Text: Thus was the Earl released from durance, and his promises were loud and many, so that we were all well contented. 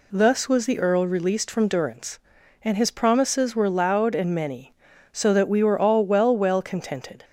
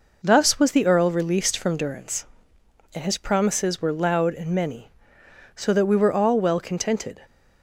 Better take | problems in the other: second | says "well" twice; at 6.3 s

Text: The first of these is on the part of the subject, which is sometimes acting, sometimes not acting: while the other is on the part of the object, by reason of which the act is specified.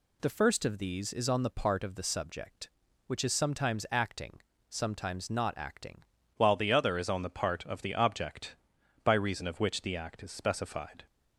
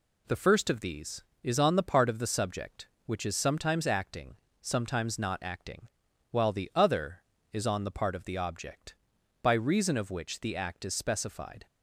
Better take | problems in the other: second | changes voice at "while"; from 6.3 s on; 4.7 s long

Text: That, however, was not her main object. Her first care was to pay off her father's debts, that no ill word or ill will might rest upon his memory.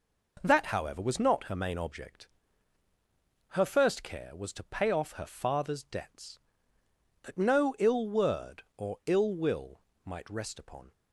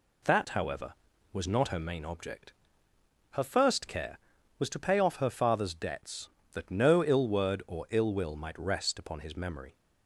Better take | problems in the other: second | pauses between "will" and "might"; slight; at 9.8 s; 0.24 s long // stops before "his memory"; at 10.9 s

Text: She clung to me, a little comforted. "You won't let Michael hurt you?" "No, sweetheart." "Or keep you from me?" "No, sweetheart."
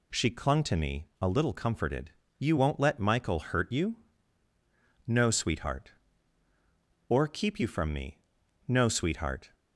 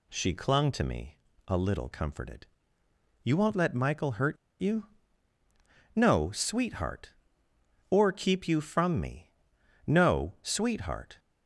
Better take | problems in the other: first | pauses between "hurt" and "you"; slight; at 4.3 s; 0.26 s long

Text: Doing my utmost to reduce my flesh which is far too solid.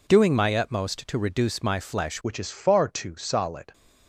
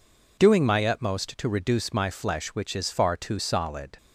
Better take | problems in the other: second | changes voice at "which"; from 2.2 s on; 1.5 s long

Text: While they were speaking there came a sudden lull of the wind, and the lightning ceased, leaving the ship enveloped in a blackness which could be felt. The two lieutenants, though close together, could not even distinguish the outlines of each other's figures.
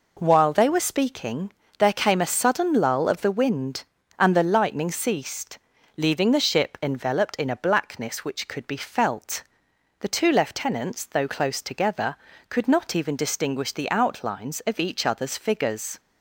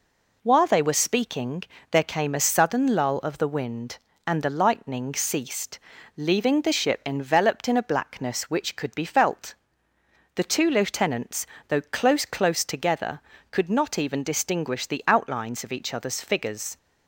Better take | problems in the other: first | pauses between "speaking" and "there"; slight; at 1.6 s; 0.26 s long; slight in the first // says "close" twice; at 12.2 s

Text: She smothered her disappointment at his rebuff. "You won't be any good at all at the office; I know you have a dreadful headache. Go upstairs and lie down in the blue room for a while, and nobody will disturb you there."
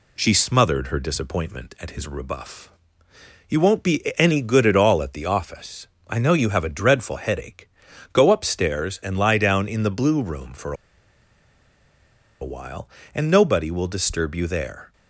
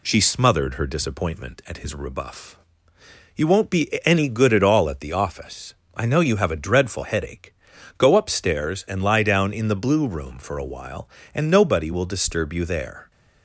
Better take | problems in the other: second | pauses between "be" and "any"; slight; at 4.0 s; 0.16 s long; slight in the second // pauses between "for" and "a"; strong; at 10.7 s; 1.6 s long

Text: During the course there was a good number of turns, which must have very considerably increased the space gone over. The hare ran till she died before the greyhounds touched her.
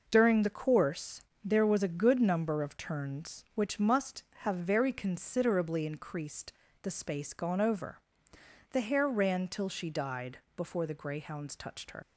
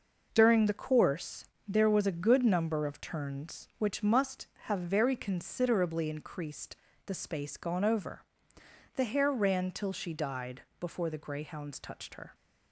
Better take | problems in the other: second | pauses between "course" and "there"; slight; at 1.2 s; 0.22 s long; slight in the second // pauses between "increased" and "the"; slight; at 6.5 s; 0.30 s long; slight in the second // pauses between "died" and "before"; slight; at 10.3 s; 0.16 s long; slight in the second // leaves "her" unfinished; at 12.0 s; 80 ms

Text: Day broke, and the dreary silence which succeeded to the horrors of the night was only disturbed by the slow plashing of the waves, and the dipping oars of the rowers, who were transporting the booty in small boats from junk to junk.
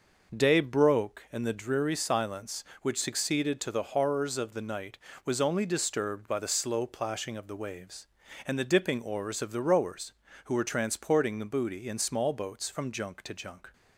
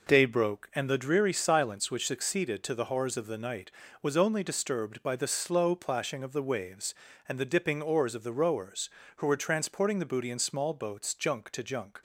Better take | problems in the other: first | skips "from"; at 11.1 s

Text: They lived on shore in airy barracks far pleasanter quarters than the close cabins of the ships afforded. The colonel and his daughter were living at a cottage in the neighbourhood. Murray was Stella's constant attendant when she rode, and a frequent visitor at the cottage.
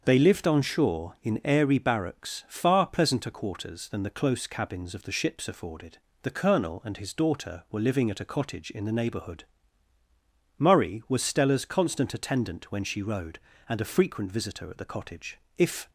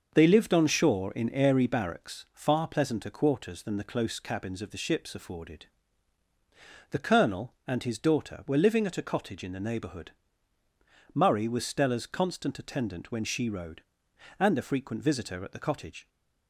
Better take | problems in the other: second | starts louder than the rest; until 1.0 s; 6.5 dB // goes on to say "If"; slight; from 15.5 s on; 0.32 s long

